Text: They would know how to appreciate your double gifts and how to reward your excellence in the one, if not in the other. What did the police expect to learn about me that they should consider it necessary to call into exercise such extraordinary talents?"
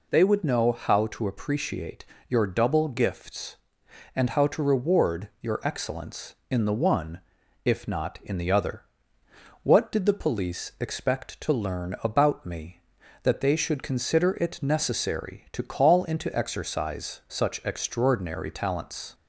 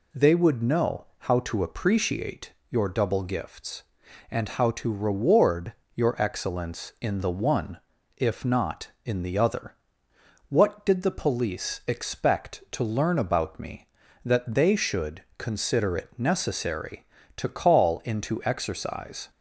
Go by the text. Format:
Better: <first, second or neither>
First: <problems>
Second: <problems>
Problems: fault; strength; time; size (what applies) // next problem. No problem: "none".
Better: first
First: pauses between "appreciate" and "your"; slight; at 2.0 s; 0.24 s long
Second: pauses between "appreciate" and "your"; slight; at 2.5 s; 0.16 s long // pauses between "reward" and "your"; slight; at 5.7 s; 0.22 s long // pauses between "should" and "consider"; slight; at 15.2 s; 0.16 s long // stops before "such extraordinary talents"; at 19.2 s